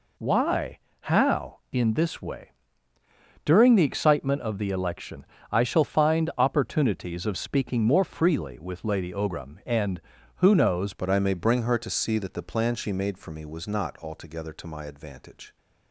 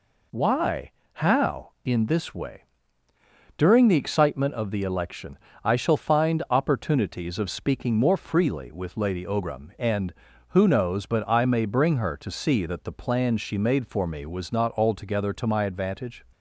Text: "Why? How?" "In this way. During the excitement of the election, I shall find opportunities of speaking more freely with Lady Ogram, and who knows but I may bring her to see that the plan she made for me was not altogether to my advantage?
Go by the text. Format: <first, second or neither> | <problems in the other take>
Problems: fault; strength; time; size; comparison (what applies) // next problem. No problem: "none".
second | changes voice at "but"; from 10.9 s on; 4.6 s long